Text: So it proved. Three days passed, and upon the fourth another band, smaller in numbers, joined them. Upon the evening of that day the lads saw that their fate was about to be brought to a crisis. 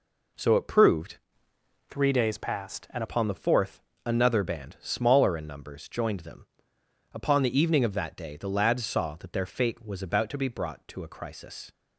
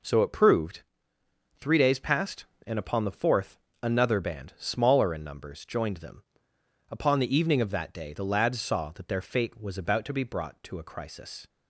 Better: second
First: changes voice from "Three" to "and"; from 1.8 to 3.0 s; 1.2 s long // pauses between "fourth" and "another"; slight; at 3.8 s; 0.24 s long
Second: pauses between "fourth" and "another"; slight; at 3.5 s; 0.24 s long

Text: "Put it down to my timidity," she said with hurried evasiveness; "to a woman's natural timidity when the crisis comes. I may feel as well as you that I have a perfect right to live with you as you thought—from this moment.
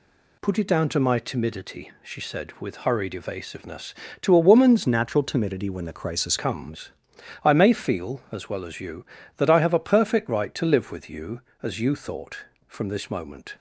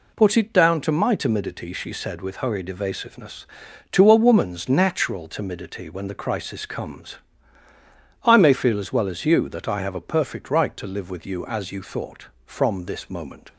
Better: second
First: changes voice from "natural" to "crisis"; from 4.8 to 6.3 s; 1.5 s long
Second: none

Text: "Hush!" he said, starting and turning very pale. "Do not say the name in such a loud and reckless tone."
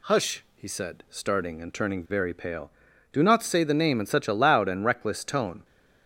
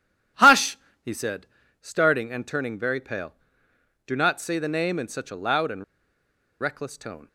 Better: first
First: none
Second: pauses between "and" and "reckless"; noticeable; at 5.8 s; 0.77 s long

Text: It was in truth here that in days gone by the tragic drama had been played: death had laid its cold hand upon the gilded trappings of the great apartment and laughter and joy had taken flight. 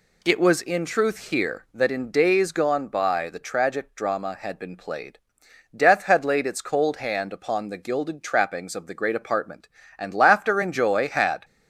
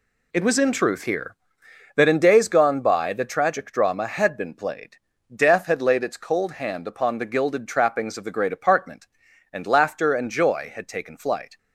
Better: second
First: stops before "taken flight"; at 11.4 s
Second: none

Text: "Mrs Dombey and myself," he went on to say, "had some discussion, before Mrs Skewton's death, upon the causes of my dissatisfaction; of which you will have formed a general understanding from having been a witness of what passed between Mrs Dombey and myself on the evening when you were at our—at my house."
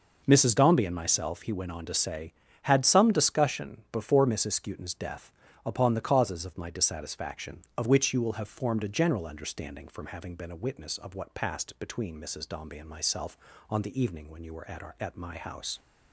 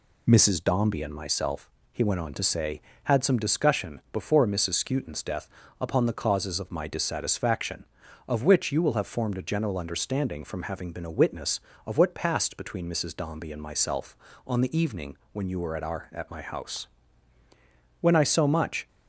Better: first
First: none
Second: pauses between "evening" and "when"; slight; at 15.1 s; 0.16 s long // goes on to say "When I so much"; noticeable; from 17.9 s on; 0.88 s long

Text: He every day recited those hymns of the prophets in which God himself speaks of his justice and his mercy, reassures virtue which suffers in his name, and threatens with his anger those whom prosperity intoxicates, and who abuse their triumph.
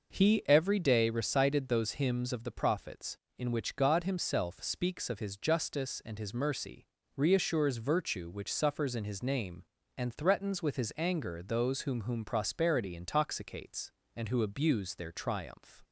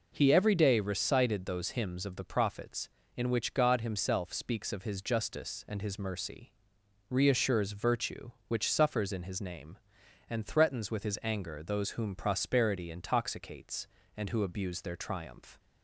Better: second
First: says "whom" twice; at 12.0 s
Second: none

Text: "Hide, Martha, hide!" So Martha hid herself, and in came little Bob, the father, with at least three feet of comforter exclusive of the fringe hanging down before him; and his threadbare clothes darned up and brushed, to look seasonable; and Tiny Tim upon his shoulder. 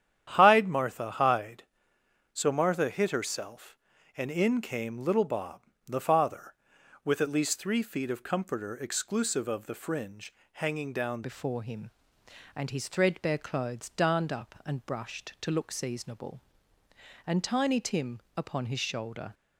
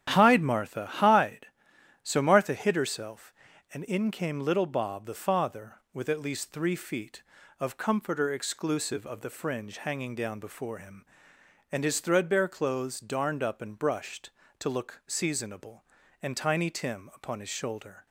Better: second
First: starts louder than the rest; strong; until 1.3 s; 10 dB // pauses between "fringe" and "hanging"; slight; at 10.3 s; 0.18 s long // changes voice at "before"; from 11.2 s on; 8.1 s long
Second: starts louder than the rest; strong; until 1.1 s; 10 dB

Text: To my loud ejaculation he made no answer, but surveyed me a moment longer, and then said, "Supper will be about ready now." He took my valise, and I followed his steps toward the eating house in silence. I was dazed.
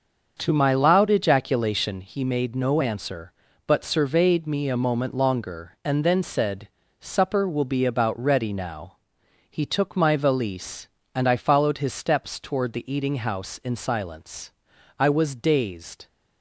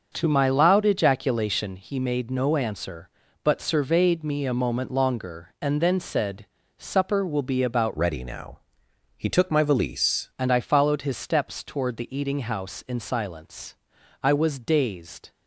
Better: first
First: starts louder than the rest; until 1.4 s; 6.5 dB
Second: starts louder than the rest; until 1.1 s; 6.5 dB // changes voice from "ready" to "valise"; from 7.9 to 10.2 s; 2.3 s long

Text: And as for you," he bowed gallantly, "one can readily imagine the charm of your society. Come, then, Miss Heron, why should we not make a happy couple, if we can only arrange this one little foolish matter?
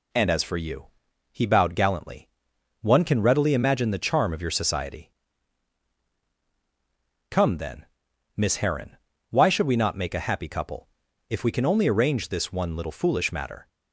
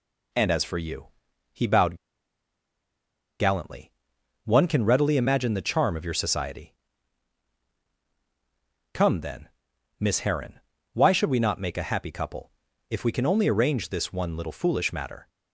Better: first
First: none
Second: pauses between "bowed" and "gallantly"; strong; at 1.9 s; 1.4 s long

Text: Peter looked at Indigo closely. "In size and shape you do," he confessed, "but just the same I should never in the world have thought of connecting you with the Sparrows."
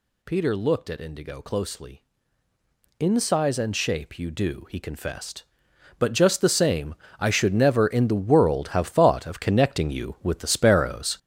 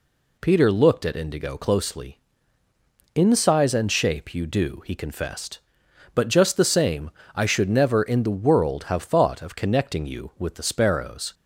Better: second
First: gets louder; strong; throughout; 9 dB // pauses between "same" and "I"; slight; at 6.9 s; 0.24 s long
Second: pauses between "same" and "I"; slight; at 7.0 s; 0.24 s long

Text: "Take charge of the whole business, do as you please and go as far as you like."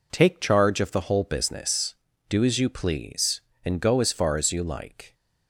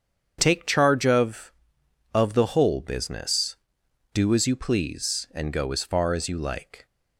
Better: first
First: none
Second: starts louder than the rest; strong; until 1.4 s; 7.5 dB // says "of" twice; at 2.1 s

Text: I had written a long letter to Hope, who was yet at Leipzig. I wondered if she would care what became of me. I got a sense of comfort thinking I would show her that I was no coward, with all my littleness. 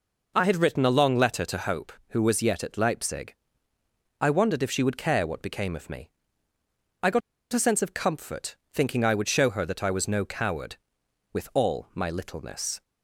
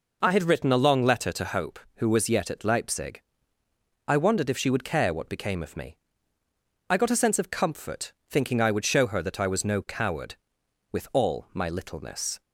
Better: second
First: pauses between "got" and "a"; slight; at 7.2 s; 0.32 s long // pauses between "comfort" and "thinking"; slight; at 8.5 s; 0.18 s long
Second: pauses between "comfort" and "thinking"; slight; at 8.1 s; 0.18 s long

